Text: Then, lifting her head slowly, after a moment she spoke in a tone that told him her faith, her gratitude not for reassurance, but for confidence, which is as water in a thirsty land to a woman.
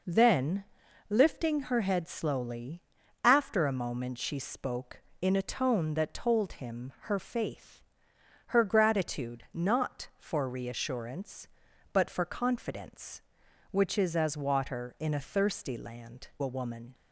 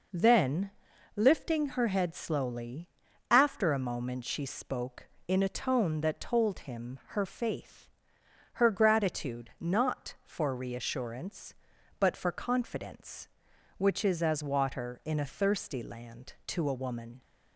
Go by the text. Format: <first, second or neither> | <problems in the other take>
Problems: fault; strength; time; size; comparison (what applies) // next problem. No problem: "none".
second | skips "to"; at 16.3 s